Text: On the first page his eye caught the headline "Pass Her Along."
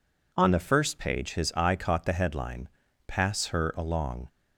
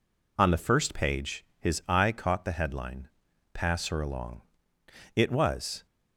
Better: first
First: pauses between "headline" and "Pass"; slight; at 2.7 s; 0.36 s long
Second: pauses between "headline" and "Pass"; noticeable; at 3.0 s; 0.46 s long // goes on to say "It was"; noticeable; from 5.1 s on; 0.70 s long

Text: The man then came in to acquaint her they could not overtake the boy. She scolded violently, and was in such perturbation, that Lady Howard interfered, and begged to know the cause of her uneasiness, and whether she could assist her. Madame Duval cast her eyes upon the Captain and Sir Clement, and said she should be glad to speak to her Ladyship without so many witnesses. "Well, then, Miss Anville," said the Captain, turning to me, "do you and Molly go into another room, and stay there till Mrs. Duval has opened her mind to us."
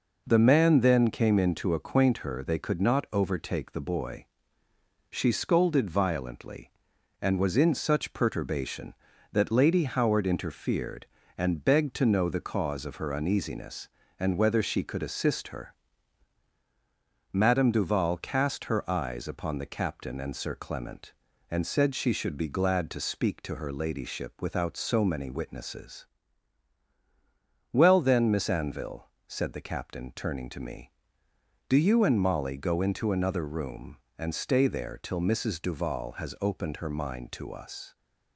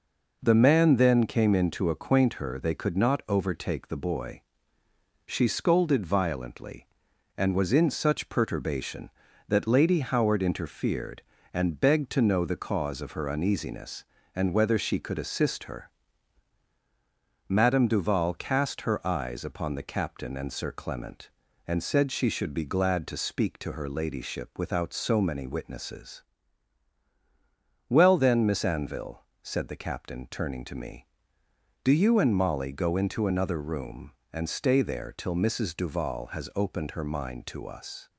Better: neither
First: none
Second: none

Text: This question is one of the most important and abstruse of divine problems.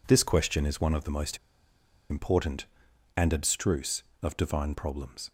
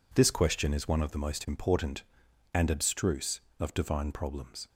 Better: second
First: pauses between "most" and "important"; noticeable; at 1.3 s; 0.73 s long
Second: none

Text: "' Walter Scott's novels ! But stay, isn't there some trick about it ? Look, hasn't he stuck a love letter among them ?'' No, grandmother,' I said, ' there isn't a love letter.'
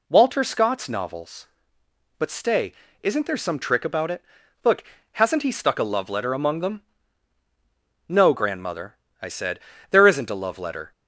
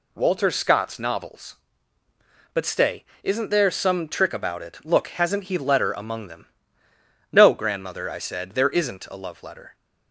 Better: first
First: none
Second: skips "stuck a love"; at 5.5 s

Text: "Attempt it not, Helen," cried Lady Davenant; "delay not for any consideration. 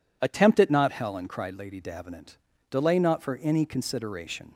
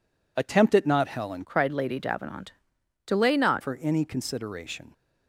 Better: first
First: none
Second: changes voice from "cried" to "not"; from 1.4 to 3.6 s; 2.2 s long

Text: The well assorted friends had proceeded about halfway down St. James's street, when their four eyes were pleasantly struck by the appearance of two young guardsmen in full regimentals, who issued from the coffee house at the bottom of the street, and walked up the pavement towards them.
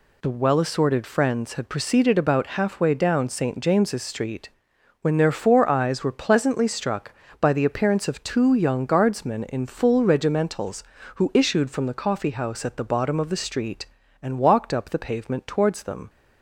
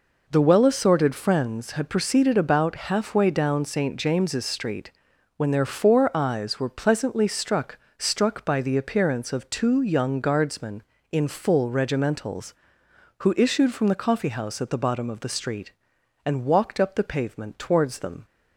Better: first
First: none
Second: says "struck" twice; at 7.9 s

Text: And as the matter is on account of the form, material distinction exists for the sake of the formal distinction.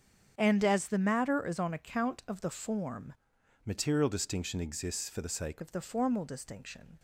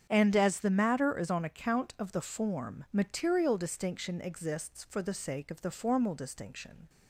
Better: second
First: starts louder than the rest; strong; until 1.3 s; 7.5 dB // changes voice from "material" to "sake"; from 3.6 to 5.6 s; 2.0 s long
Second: starts louder than the rest; strong; until 1.1 s; 8 dB

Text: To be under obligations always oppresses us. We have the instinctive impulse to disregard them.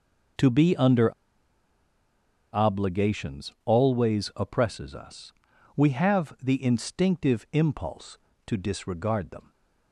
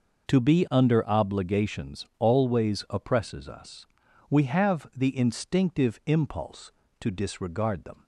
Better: second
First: pauses between "under" and "obligations"; strong; at 1.1 s; 1.4 s long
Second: none

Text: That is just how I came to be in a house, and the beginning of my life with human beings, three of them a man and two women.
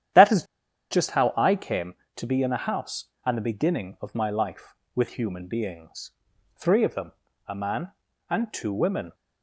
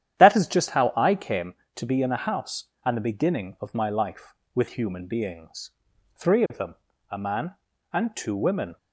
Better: second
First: starts louder than the rest; strong; until 1.6 s; 10.5 dB // pauses between "is" and "just"; noticeable; at 0.4 s; 0.47 s long // pauses between "them" and "a"; slight; at 7.1 s; 0.34 s long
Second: starts louder than the rest; strong; until 1.2 s; 10.5 dB // pauses between "them" and "a"; slight; at 6.7 s; 0.34 s long

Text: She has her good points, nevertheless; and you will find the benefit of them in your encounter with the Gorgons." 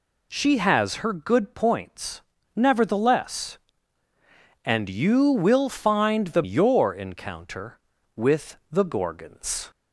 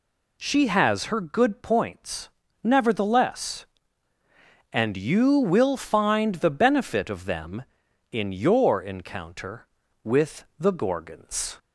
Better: second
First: skips "benefit of them in"; at 6.4 s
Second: none

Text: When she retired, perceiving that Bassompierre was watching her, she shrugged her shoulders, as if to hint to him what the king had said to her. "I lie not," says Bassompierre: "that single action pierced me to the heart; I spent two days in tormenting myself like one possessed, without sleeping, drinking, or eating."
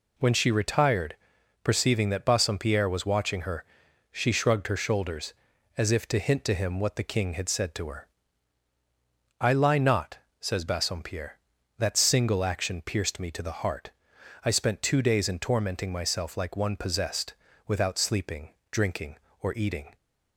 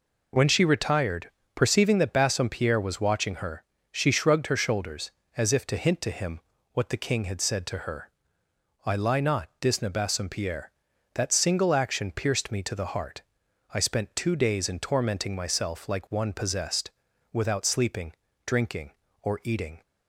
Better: first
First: none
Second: pauses between "him" and "what"; slight; at 6.4 s; 0.32 s long // says "disna" for "says"; at 9.6 s

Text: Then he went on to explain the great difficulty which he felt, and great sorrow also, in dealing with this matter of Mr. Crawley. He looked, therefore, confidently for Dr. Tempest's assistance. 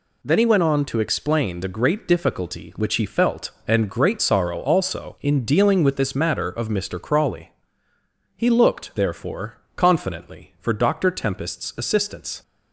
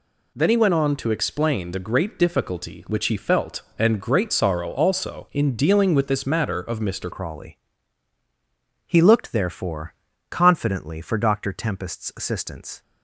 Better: first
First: none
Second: changes voice at "Crawley"; from 7.1 s on; 5.7 s long

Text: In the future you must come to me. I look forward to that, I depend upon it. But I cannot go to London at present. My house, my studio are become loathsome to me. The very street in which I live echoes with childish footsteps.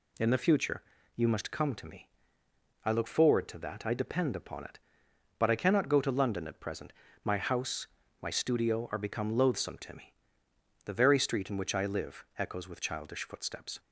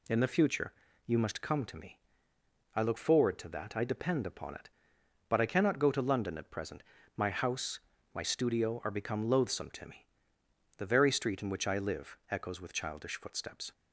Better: neither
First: pauses between "future" and "you"; slight; at 0.8 s; 0.34 s long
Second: pauses between "future" and "you"; slight; at 0.7 s; 0.34 s long

